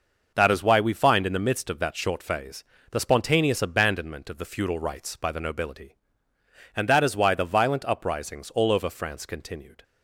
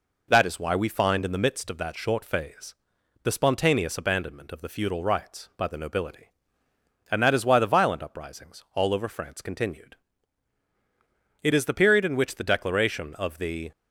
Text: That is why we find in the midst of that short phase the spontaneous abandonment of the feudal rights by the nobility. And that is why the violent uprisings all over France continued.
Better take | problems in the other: first | pauses between "phase" and "the"; noticeable; at 2.7 s; 0.48 s long; slight in the first // goes on to say "It is the period in which the Declaration of the"; strong; from 11.4 s on; 2.3 s long

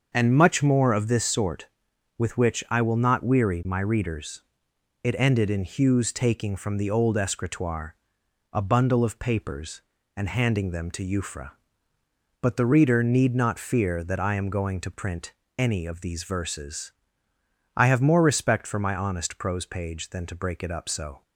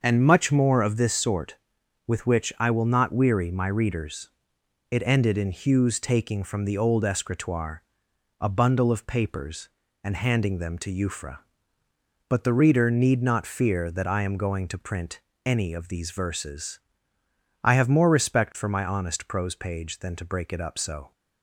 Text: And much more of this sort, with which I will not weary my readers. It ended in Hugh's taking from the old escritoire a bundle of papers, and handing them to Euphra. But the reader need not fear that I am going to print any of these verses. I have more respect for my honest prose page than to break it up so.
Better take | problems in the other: neither | starts louder than the rest; the same in both // pauses between "escritoire" and "a"; noticeable; the same in both // pauses between "print" and "any"; slight; the same in both

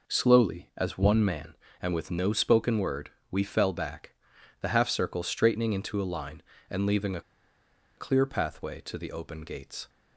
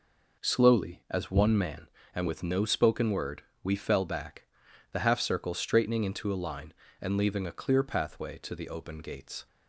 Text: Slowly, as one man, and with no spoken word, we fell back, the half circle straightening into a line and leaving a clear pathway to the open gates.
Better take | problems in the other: second | pauses between "a" and "clear"; noticeable; at 7.2 s; 0.75 s long

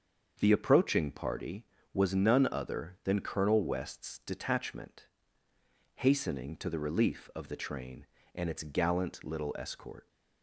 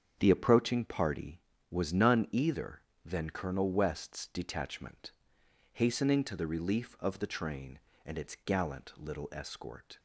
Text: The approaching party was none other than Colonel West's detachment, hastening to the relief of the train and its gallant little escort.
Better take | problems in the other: first | starts louder than the rest; strong; until 1.1 s; 7.5 dB; also in the first // says "either" for "other"; at 2.3 s

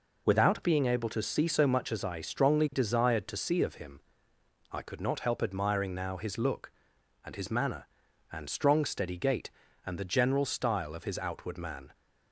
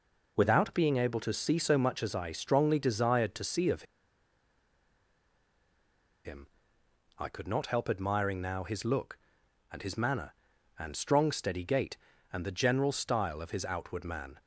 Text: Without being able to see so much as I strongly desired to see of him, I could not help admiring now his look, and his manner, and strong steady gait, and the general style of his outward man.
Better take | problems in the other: first | pauses between "of" and "him"; strong; at 3.8 s; 2.4 s long

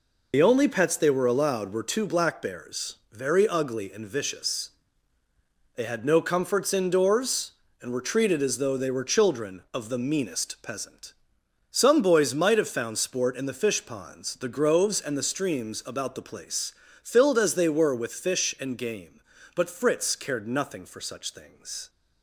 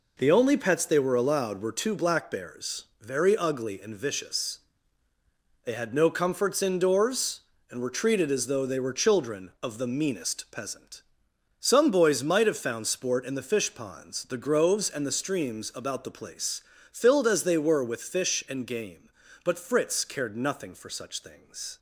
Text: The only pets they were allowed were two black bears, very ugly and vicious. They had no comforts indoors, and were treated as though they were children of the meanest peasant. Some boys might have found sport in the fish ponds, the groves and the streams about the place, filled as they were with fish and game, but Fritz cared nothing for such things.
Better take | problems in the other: second | loses the start of "The"; at 0.3 s; 45 ms

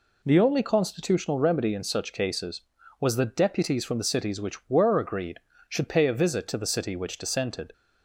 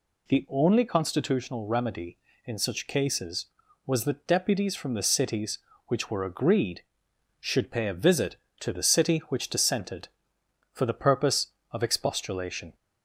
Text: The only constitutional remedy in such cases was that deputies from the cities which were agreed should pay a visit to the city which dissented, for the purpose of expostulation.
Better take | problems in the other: second | stops before "for the purpose of expostulation"; at 7.7 s

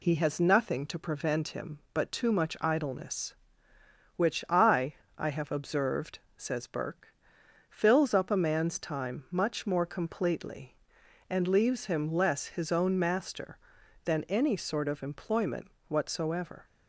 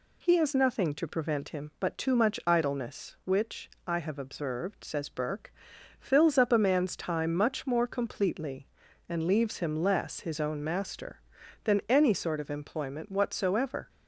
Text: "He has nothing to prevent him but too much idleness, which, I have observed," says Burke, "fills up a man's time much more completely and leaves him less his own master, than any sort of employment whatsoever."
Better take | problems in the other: second | says "I" twice; at 5.1 s // pauses between "employment" and "whatsoever"; slight; at 15.7 s; 0.16 s long

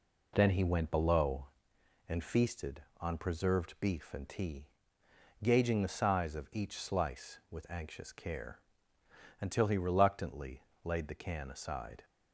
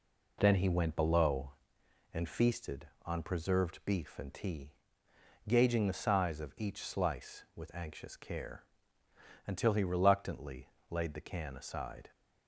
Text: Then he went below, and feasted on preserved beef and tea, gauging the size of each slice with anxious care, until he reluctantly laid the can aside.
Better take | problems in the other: neither | pauses between "reluctantly" and "laid"; slight; the same in both

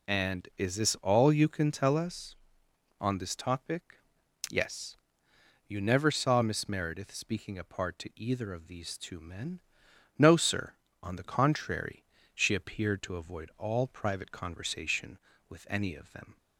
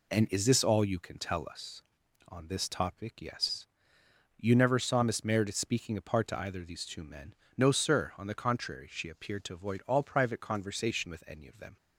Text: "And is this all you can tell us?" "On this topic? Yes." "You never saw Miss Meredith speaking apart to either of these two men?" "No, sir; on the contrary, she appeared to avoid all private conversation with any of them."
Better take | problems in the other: neither | none

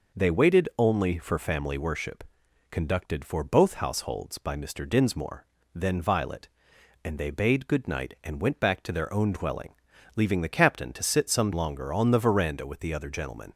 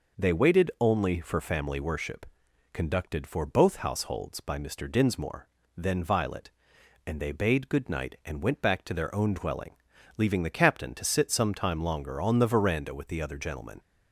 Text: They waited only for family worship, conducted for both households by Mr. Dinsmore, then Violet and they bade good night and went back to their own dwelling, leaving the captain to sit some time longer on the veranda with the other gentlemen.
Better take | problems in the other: second | skips "time"; at 11.5 s

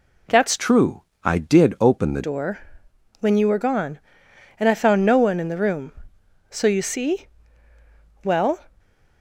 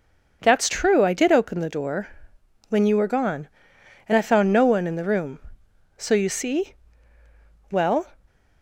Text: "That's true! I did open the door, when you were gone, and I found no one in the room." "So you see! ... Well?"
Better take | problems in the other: second | changes voice from "true" to "the"; from 0.5 to 2.2 s; 1.7 s long // stays silent after the last word; slight; from 8.6 s on; 0.6 s long

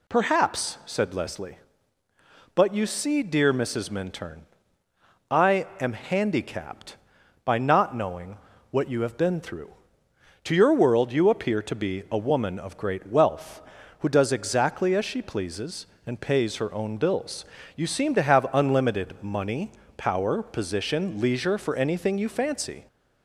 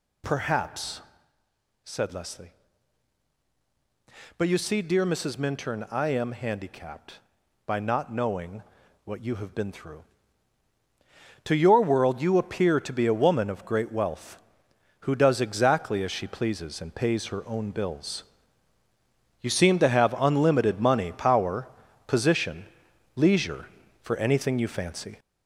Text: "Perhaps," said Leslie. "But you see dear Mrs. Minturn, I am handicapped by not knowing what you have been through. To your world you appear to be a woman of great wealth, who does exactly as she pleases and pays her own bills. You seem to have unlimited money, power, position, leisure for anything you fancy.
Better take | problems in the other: first | gets louder; noticeable; throughout; 4.5 dB // pauses between "knowing" and "what"; at 8.6 s; 0.42 s long; slight in the first

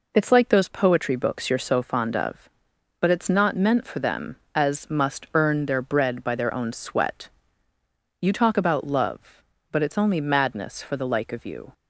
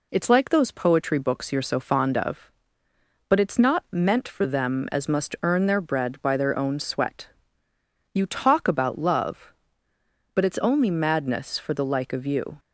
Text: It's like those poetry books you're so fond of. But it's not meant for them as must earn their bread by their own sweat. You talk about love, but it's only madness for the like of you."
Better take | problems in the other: neither | none

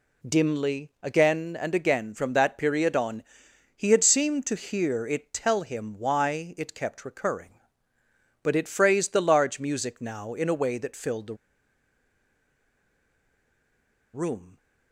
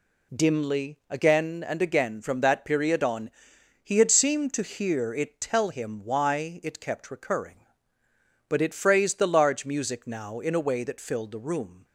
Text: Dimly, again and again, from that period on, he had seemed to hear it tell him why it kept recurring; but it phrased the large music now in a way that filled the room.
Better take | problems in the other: second | pauses between "the" and "room"; strong; at 11.3 s; 2.7 s long

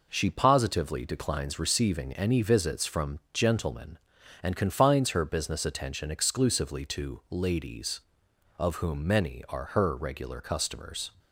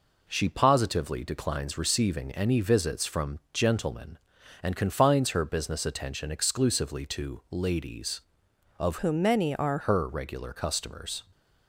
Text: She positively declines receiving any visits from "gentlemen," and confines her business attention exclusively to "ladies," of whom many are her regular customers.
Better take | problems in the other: first | changes voice from "whom" to "are"; from 8.9 to 9.7 s; 0.8 s long

